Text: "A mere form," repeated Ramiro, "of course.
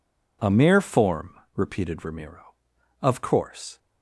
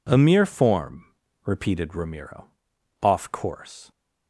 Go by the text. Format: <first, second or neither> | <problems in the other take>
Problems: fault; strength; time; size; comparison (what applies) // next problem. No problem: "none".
first | says "off" for "of"; at 3.0 s